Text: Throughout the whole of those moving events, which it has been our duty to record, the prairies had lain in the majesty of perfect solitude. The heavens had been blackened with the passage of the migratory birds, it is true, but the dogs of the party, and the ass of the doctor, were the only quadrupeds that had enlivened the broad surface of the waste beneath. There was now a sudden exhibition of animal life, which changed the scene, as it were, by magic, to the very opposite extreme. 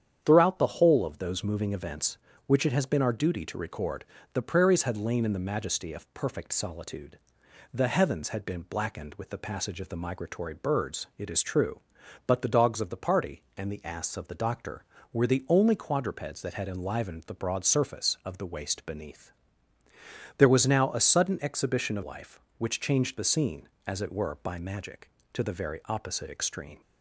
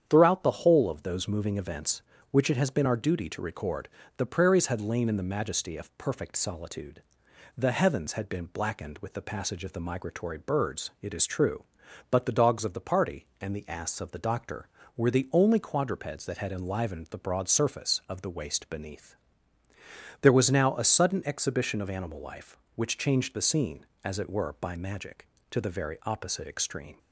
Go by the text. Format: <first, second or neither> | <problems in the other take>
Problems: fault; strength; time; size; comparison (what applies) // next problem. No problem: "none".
second | starts louder than the rest; strong; until 1.2 s; 8.5 dB; strong in the second // skips "animal"; at 22.0 s